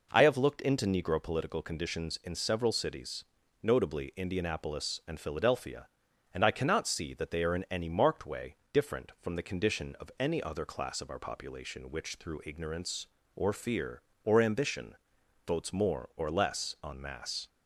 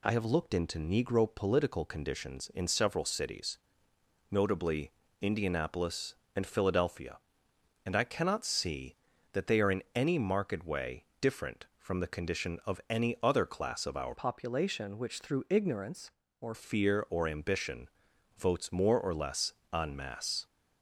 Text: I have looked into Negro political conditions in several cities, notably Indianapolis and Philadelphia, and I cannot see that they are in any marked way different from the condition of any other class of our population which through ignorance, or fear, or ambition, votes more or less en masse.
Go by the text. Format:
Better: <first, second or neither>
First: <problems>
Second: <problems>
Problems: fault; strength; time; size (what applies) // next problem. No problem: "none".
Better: first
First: pauses between "way" and "different"; slight; at 8.5 s; 0.16 s long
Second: pauses between "notably" and "Indianapolis"; slight; at 4.9 s; 0.30 s long // pauses between "way" and "different"; slight; at 11.0 s; 0.18 s long // changes voice from "population" to "or"; from 14.1 to 16.5 s; 2.4 s long // pauses between "less" and "en"; slight; at 19.5 s; 0.20 s long